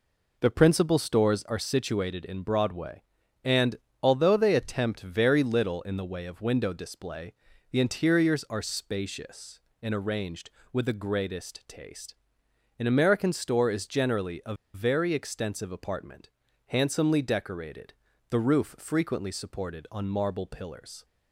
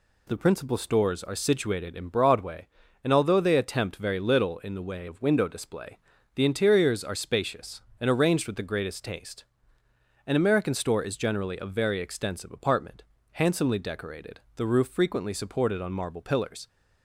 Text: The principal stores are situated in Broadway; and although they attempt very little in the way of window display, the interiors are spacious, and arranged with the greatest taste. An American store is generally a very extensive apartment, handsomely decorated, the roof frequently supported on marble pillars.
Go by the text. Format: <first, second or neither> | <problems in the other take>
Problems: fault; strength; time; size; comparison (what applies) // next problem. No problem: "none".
second | pauses between "and" and "although"; slight; at 3.7 s; 0.28 s long // pauses between "a" and "very"; slight; at 14.5 s; 0.20 s long